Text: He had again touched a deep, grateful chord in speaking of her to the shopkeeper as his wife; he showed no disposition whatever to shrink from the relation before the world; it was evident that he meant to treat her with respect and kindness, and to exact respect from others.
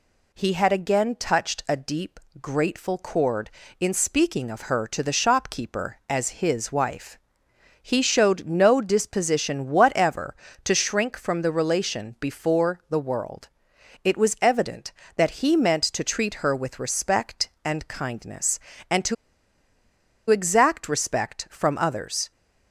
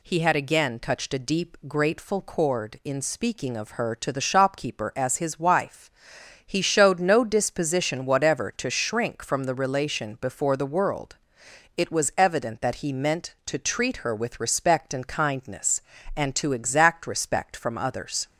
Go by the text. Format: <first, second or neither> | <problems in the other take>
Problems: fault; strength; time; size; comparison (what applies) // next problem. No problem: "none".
second | pauses between "to" and "exact"; at 19.1 s; 1.1 s long